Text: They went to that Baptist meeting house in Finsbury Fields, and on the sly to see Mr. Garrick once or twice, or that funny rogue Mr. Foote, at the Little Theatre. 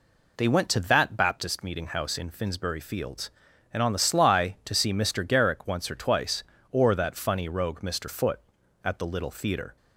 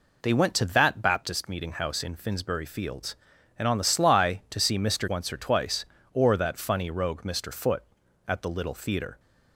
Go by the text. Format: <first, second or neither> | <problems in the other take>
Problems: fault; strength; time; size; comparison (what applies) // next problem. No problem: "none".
first | skips "Garrick"; at 5.0 s